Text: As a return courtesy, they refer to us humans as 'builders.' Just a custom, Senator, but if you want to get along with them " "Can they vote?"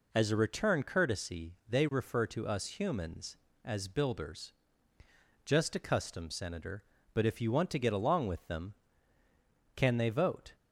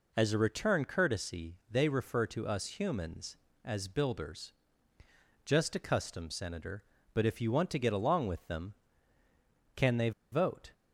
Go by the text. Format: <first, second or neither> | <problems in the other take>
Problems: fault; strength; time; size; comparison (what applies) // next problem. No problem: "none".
first | pauses between "they" and "vote"; slight; at 10.1 s; 0.21 s long